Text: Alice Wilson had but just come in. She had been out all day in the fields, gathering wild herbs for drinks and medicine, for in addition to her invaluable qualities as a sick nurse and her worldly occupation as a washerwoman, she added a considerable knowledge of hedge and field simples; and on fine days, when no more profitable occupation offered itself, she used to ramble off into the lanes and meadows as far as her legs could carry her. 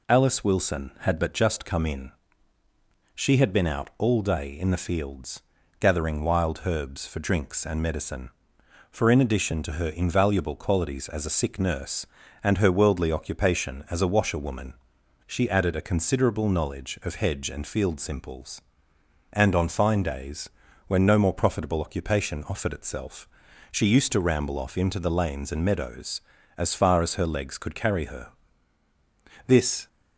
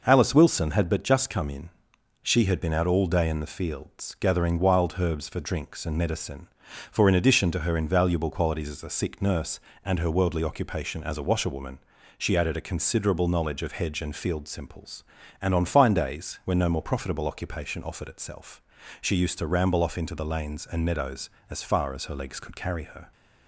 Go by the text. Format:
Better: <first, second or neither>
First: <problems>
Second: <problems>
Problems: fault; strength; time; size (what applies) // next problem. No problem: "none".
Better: second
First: goes on to say "This"; slight; from 29.4 s on; 0.42 s long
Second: none